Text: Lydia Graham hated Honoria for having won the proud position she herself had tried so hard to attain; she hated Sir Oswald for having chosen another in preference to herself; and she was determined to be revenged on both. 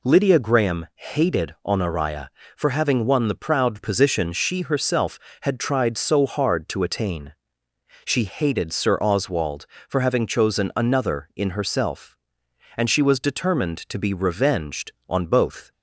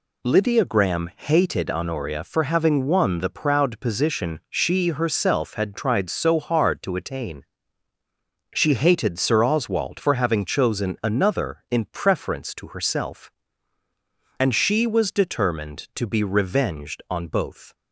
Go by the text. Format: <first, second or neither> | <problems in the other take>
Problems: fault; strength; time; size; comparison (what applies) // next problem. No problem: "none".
second | skips "preference to"; at 11.5 s